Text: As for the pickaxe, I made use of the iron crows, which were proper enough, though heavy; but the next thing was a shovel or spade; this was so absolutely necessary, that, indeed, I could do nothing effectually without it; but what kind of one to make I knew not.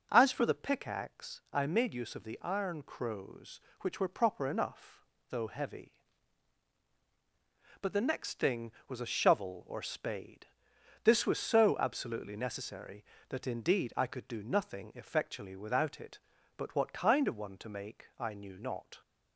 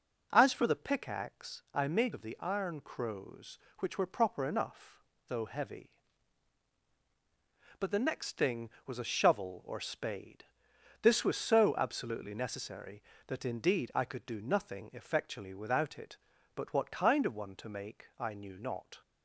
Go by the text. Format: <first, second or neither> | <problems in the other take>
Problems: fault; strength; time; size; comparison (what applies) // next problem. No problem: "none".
first | skips "use"; at 2.1 s